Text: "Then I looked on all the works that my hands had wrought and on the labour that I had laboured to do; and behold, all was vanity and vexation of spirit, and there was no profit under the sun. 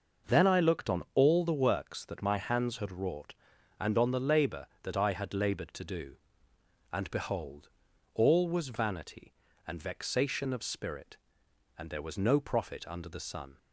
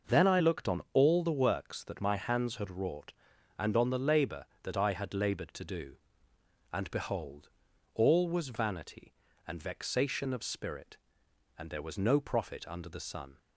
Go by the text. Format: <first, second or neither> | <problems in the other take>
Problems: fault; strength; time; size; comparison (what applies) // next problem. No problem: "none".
neither | none